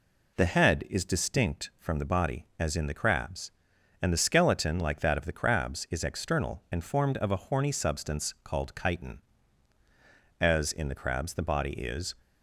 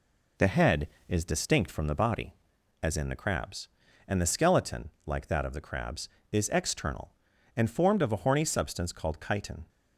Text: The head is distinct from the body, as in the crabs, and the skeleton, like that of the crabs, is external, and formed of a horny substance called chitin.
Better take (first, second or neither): second